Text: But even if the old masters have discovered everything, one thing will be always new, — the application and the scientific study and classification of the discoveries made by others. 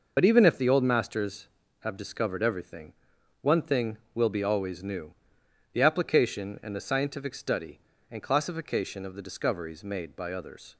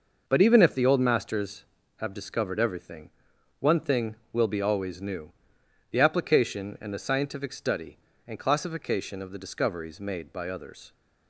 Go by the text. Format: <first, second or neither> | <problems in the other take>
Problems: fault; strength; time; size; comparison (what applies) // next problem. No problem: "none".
second | loses the start of "But"; at 0.1 s; 55 ms